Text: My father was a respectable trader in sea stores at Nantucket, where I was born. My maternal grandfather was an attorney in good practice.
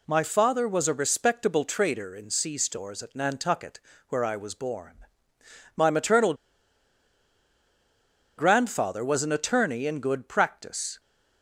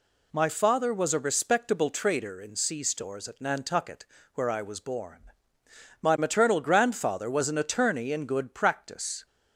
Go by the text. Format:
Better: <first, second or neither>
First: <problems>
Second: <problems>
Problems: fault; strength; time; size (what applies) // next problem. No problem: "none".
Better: second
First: pauses between "maternal" and "grandfather"; strong; at 6.3 s; 2.0 s long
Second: none